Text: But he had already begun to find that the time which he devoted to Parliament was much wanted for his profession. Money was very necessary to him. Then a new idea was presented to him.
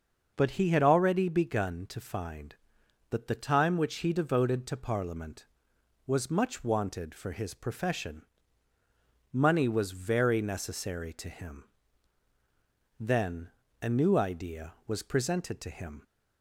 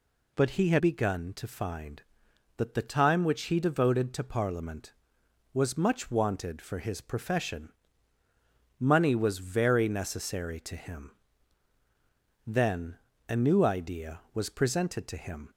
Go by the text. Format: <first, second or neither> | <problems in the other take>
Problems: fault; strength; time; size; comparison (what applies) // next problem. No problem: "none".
first | skips "already"; at 0.7 s // pauses between "Then" and "a"; slight; at 12.9 s; 0.32 s long; slight in the first